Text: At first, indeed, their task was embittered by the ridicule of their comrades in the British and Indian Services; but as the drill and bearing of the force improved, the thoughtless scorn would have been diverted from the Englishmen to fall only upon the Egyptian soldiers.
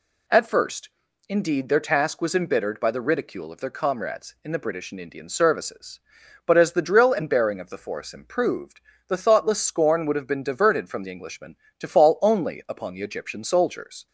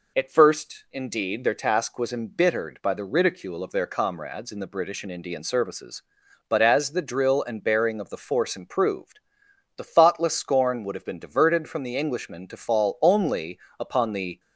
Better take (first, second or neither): first